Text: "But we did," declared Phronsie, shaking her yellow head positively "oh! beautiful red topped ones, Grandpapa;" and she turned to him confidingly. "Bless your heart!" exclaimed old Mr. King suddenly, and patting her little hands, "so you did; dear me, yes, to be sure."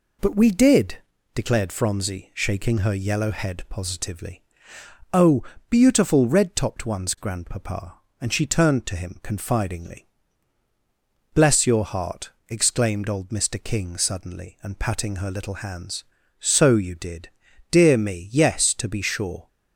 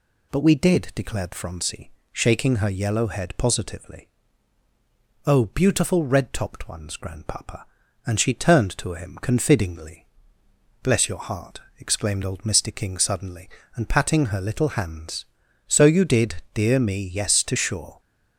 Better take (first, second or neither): first